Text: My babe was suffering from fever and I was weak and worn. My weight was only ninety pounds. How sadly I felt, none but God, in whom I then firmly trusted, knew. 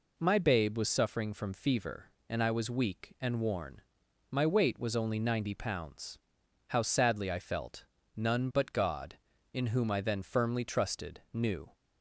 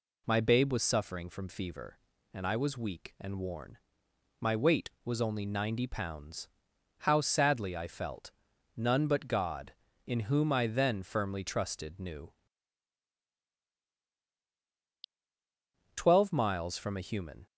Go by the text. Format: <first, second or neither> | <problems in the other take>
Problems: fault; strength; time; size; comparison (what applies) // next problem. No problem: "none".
first | goes on to say "Twelve miles from a human"; from 15.9 s on; 1.5 s long